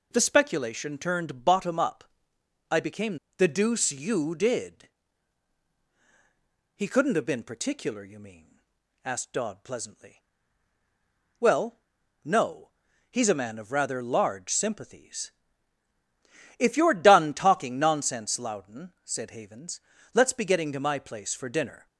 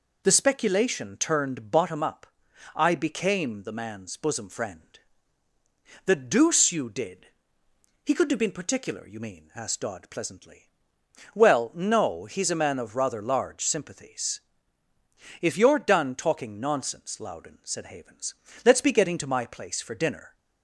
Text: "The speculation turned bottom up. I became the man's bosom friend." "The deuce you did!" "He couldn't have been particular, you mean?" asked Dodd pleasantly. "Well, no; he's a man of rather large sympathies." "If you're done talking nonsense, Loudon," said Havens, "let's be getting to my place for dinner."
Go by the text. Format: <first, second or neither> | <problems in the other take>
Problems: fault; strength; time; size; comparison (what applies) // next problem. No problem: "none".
second | skips "the man's bosom friend"; at 3.2 s